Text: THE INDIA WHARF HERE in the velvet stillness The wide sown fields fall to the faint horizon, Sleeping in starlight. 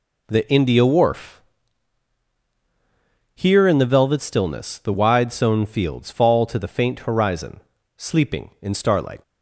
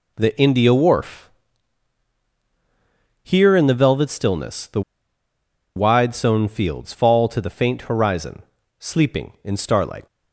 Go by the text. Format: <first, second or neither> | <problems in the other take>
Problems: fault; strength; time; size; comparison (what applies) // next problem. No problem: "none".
first | pauses between "WHARF" and "HERE"; strong; at 1.3 s; 1.9 s long; strong in the first // pauses between "The" and "wide"; noticeable; at 4.8 s; 0.94 s long